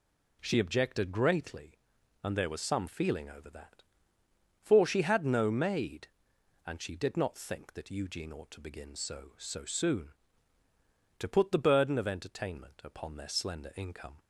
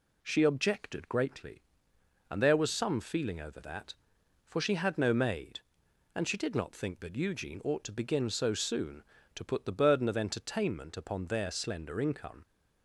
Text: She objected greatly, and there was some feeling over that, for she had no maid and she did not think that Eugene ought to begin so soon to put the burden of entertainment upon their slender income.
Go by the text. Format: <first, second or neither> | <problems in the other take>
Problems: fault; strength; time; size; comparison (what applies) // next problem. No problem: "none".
second | says "so" twice; at 9.3 s